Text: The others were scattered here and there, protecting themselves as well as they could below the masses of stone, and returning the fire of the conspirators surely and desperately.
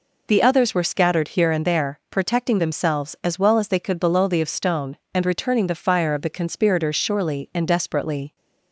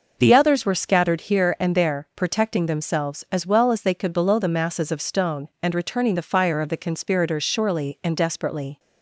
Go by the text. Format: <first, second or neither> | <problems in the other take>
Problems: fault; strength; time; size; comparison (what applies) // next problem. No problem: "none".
second | skips "masses"; at 4.4 s